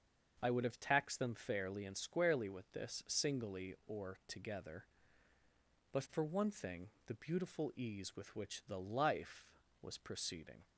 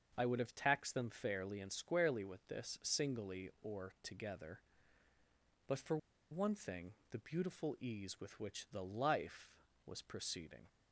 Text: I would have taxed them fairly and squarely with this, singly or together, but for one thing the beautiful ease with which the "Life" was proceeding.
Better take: first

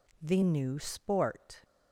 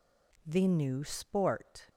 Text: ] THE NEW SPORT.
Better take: neither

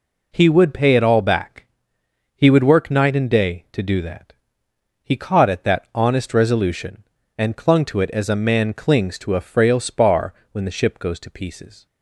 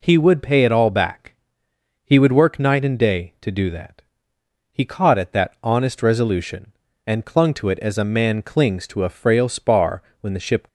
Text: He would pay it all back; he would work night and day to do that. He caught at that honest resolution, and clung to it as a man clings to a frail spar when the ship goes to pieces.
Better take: first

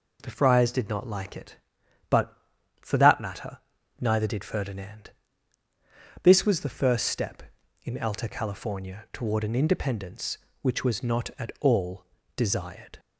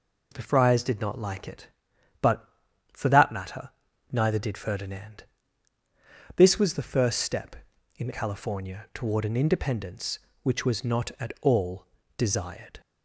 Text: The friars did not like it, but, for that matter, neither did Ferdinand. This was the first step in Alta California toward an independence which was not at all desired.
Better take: first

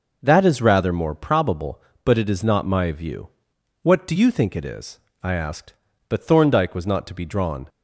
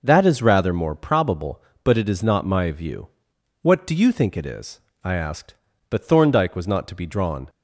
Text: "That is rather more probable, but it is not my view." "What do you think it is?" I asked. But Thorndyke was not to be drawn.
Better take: neither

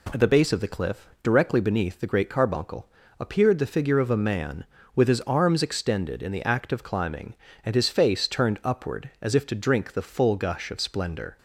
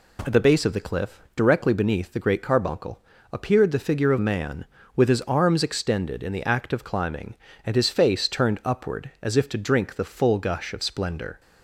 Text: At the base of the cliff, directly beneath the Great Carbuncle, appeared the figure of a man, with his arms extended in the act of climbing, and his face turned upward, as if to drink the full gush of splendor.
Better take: first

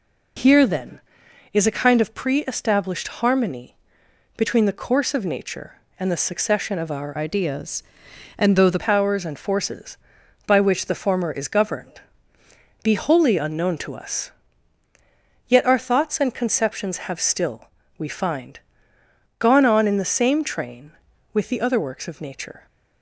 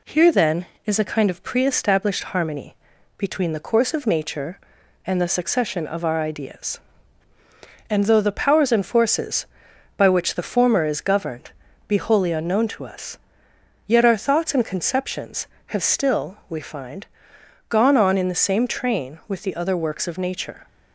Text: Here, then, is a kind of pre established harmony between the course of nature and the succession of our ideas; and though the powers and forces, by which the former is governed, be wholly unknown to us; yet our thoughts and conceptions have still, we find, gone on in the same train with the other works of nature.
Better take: second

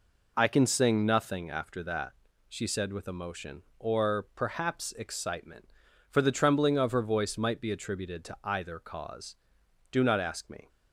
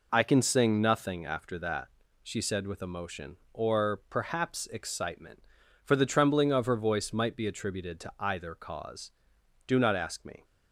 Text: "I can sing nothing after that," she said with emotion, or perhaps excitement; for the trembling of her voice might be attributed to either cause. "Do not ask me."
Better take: neither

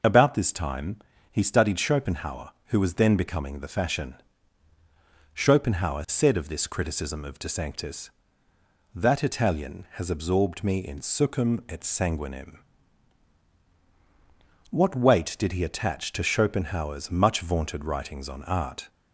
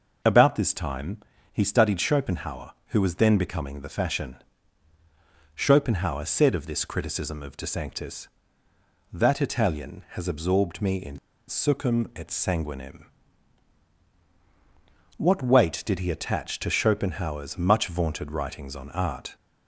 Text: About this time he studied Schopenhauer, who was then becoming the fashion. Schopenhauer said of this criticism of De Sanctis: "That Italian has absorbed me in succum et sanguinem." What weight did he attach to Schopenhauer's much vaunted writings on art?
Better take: first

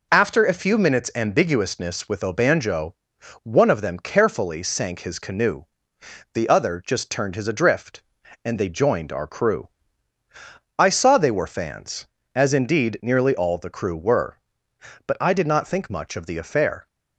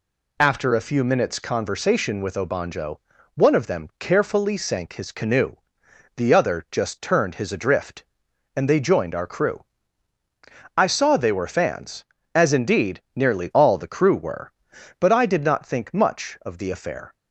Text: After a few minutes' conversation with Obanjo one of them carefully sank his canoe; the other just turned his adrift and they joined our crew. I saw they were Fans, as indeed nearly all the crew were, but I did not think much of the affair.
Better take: second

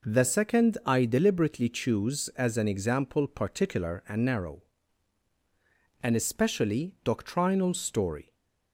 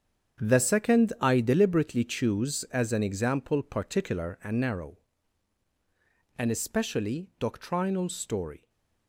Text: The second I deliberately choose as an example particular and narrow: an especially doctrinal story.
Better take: first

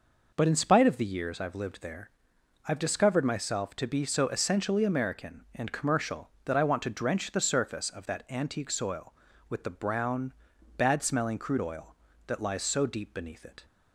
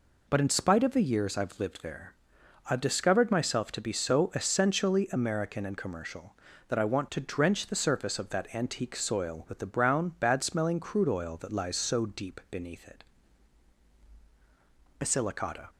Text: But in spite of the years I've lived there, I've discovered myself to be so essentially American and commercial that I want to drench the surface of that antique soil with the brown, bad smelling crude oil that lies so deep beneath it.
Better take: first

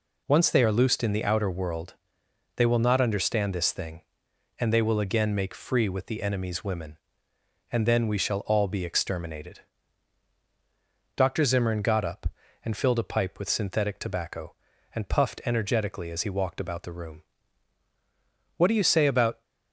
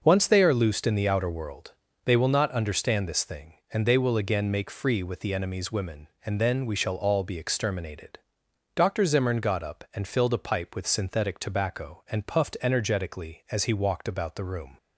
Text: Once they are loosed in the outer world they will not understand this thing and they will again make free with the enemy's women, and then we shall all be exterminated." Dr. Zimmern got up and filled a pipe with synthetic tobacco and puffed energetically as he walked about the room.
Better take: second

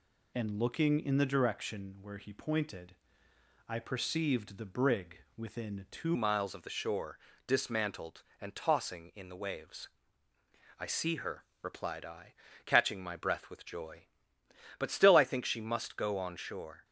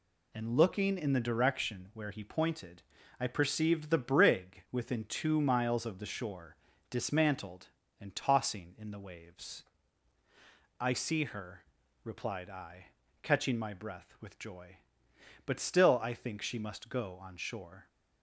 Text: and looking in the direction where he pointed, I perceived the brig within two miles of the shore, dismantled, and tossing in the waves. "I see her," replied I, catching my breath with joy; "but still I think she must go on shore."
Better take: second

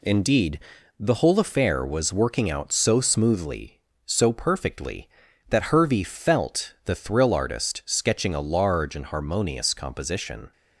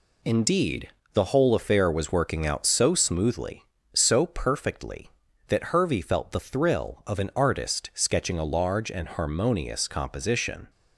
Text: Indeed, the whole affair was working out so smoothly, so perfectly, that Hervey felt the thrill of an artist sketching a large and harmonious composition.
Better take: second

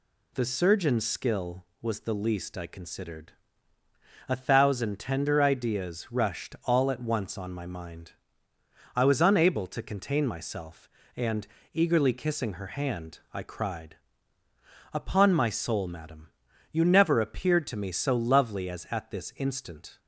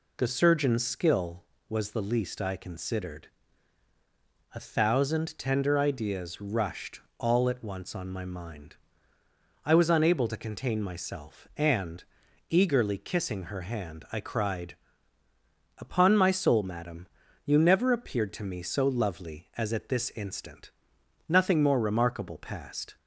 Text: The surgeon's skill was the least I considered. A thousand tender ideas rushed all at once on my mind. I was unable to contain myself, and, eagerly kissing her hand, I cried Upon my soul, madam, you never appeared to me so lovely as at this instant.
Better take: first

